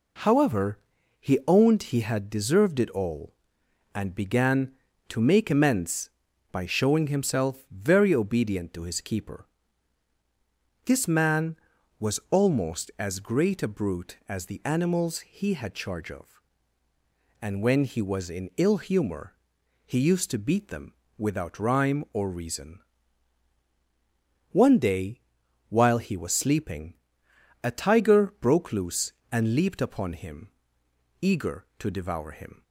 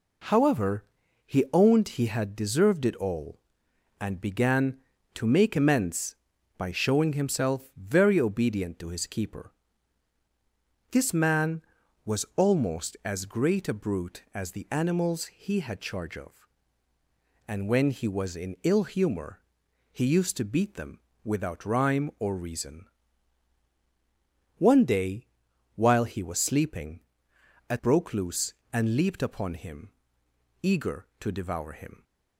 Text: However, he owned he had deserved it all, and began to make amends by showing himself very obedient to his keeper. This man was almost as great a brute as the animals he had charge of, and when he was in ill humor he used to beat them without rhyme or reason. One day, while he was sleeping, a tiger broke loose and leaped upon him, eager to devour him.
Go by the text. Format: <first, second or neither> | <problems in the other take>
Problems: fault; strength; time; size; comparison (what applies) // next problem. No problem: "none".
first | pauses between "humor" and "he"; noticeable; at 19.4 s; 0.50 s long; noticeable in the first // pauses between "them" and "without"; slight; at 21.0 s; 0.24 s long; slight in the first // skips "tiger"; at 27.7 s